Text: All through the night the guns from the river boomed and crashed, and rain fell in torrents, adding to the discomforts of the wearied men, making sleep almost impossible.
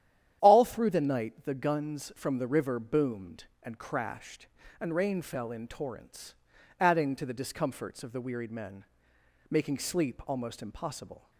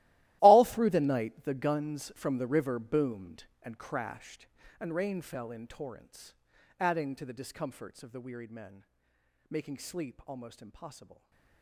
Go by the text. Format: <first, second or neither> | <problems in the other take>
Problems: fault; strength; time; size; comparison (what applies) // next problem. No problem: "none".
first | gets quieter; strong; throughout; 17.5 dB // starts louder than the rest; strong; until 1.4 s; 16.5 dB; strong in the first